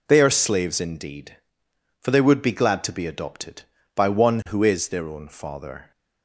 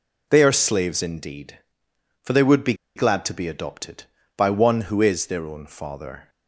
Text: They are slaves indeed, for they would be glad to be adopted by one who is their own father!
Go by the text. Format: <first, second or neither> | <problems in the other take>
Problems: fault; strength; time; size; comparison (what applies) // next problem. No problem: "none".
first | pauses between "be" and "glad"; slight; at 2.7 s; 0.22 s long